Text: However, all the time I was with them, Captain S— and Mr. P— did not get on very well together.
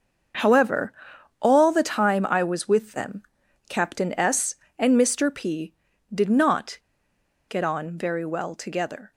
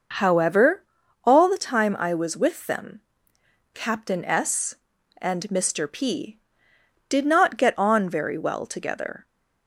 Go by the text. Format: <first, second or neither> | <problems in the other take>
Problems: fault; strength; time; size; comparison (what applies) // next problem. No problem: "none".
second | starts louder than the rest; until 1.8 s; 6.5 dB // pauses between "not" and "get"; noticeable; at 6.7 s; 0.70 s long